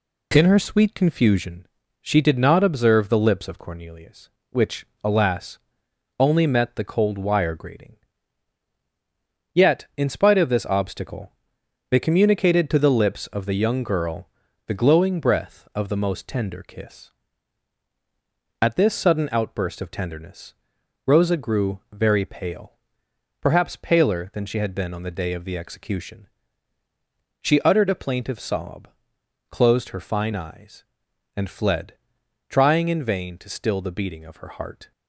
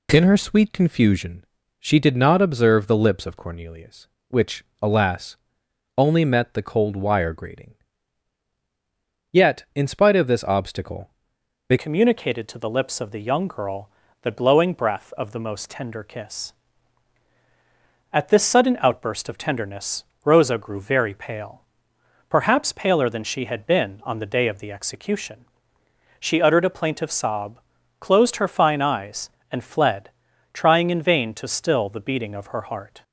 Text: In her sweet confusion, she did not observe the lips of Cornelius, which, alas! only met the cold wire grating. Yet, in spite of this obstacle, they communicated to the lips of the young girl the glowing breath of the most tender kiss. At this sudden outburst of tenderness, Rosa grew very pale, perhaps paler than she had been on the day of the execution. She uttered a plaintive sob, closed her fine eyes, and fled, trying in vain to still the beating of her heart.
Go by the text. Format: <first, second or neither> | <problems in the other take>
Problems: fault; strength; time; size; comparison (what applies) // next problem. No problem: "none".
first | changes voice at "communicated"; from 11.7 s on; 21.3 s long // pauses between "girl" and "the"; slight; at 13.8 s; 0.34 s long; slight in the first